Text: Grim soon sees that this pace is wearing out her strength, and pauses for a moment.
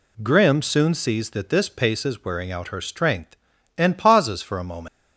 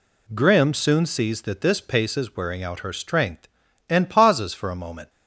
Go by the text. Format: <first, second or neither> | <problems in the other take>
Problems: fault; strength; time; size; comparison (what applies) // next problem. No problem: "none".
second | leaves "moment" unfinished; at 4.8 s; 95 ms